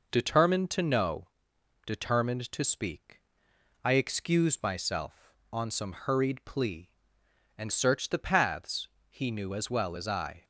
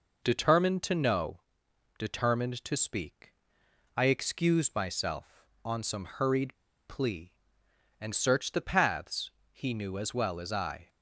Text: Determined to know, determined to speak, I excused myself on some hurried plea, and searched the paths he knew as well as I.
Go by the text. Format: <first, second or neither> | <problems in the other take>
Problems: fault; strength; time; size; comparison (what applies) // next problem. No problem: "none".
first | pauses between "hurried" and "plea"; slight; at 6.5 s; 0.31 s long // pauses between "paths" and "he"; slight; at 9.3 s; 0.20 s long; slight in the first